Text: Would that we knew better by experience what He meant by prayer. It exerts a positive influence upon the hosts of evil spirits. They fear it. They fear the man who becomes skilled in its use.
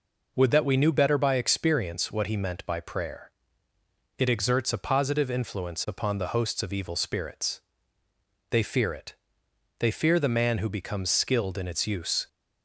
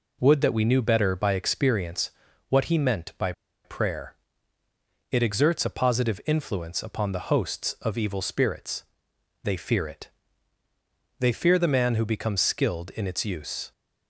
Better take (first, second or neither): first